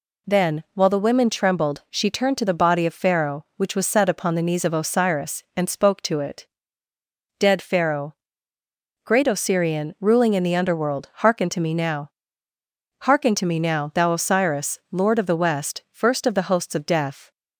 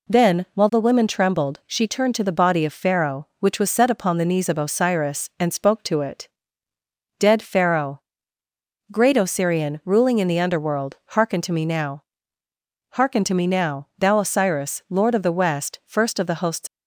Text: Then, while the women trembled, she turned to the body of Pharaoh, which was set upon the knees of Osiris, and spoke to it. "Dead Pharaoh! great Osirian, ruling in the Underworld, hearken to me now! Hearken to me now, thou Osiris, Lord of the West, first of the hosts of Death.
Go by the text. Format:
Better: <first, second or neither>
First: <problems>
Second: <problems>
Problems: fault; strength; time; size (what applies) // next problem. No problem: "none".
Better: first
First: none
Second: stops before "of Death"; at 16.6 s